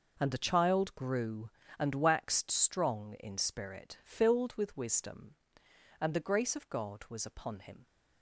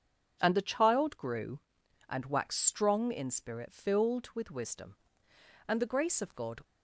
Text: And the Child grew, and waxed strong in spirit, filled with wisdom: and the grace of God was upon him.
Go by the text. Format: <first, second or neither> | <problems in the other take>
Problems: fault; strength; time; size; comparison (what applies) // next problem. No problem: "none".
first | stops before "was upon him"; at 6.6 s